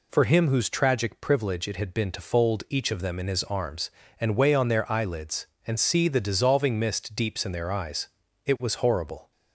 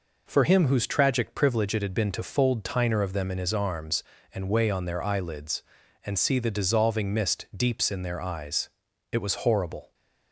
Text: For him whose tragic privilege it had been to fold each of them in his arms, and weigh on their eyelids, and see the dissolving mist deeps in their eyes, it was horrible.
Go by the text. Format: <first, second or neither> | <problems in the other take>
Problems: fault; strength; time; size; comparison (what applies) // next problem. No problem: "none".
first | says "tiner" for "each"; at 2.6 s